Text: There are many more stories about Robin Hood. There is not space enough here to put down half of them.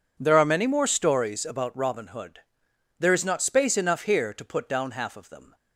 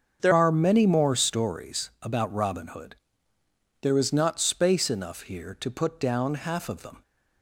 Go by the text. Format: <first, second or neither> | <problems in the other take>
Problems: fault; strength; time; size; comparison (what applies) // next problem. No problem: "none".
first | starts louder than the rest; until 1.2 s; 6.5 dB // changes voice at "are"; from 0.3 s on; 6.7 s long